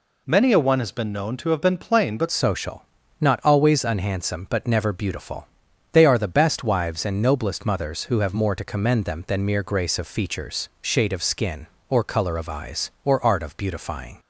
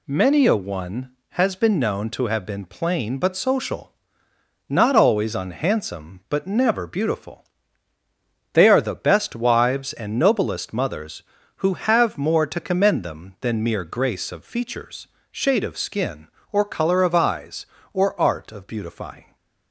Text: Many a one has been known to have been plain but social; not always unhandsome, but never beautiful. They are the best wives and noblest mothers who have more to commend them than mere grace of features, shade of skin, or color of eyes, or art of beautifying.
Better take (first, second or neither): second